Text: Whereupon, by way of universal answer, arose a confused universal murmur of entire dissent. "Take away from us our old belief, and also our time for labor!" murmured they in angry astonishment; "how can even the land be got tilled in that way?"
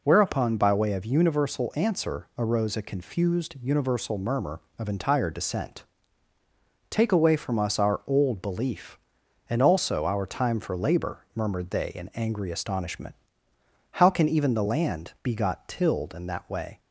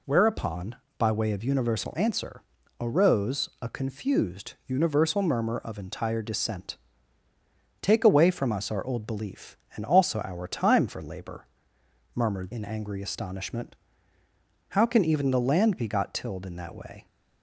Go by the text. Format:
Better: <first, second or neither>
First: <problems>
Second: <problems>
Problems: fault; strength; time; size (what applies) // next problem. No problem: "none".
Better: first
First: none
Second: skips "they"; at 12.5 s